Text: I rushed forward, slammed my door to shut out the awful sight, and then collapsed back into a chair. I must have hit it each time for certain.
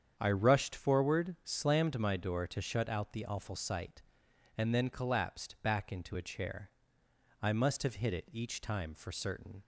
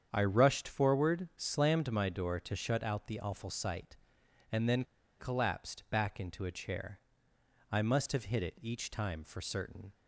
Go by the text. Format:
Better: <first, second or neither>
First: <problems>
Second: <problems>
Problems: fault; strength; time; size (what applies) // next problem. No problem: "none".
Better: first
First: starts louder than the rest; strong; until 1.1 s; 8 dB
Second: starts louder than the rest; strong; until 1.1 s; 8 dB // pauses between "then" and "collapsed"; slight; at 4.8 s; 0.36 s long